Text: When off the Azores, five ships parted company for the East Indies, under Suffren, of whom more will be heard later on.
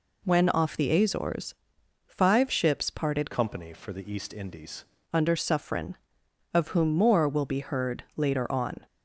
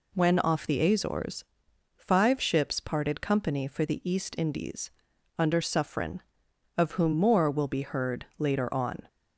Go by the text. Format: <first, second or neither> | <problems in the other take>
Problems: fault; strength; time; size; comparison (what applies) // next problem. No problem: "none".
second | changes voice from "company" to "Indies"; from 3.3 to 4.8 s; 1.5 s long